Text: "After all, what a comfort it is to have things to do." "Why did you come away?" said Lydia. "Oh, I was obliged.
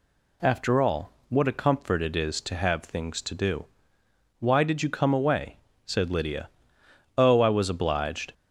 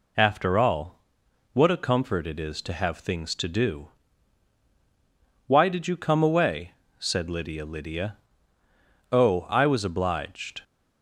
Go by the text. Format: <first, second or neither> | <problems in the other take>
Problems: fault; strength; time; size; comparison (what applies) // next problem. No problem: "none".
first | says "Lydia" twice; at 7.6 s